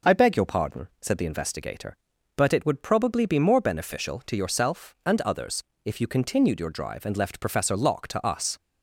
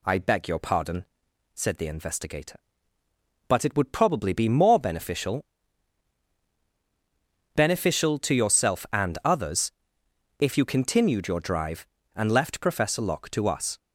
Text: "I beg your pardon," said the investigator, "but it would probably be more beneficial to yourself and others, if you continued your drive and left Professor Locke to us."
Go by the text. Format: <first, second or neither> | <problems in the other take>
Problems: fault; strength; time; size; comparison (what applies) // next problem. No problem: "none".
first | says "beneficial" twice; at 7.5 s